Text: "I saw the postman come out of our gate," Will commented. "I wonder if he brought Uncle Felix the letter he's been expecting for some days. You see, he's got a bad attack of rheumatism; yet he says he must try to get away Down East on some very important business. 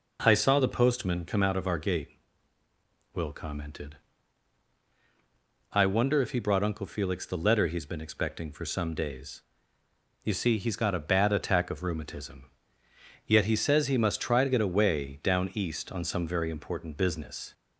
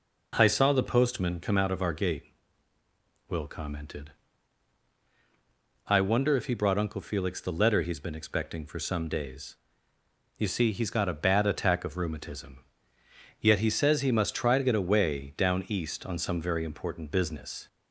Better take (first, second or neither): neither